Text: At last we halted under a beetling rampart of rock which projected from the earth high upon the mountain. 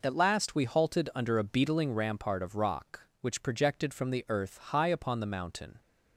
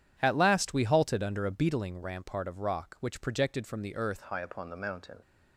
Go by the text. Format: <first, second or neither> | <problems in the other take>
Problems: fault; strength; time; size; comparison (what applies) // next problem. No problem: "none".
first | changes voice at "high"; from 4.2 s on; 1.0 s long